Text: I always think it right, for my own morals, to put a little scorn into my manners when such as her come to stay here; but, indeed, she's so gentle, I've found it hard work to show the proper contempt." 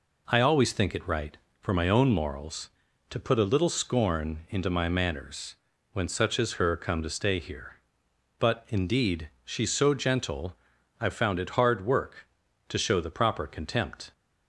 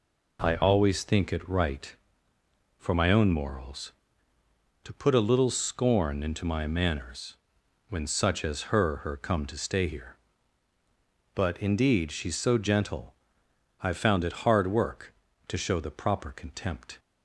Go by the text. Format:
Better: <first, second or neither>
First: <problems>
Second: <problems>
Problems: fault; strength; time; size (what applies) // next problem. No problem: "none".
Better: first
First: pauses between "manners" and "when"; at 5.5 s; 0.38 s long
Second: pauses between "manners" and "when"; noticeable; at 7.3 s; 0.56 s long // says "her" twice; at 9.0 s